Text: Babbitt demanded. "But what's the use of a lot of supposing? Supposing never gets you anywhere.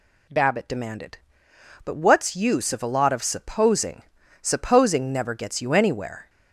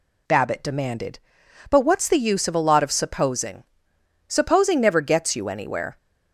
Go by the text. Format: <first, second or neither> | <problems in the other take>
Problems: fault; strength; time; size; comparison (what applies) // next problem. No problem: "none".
second | skips "the"; at 2.3 s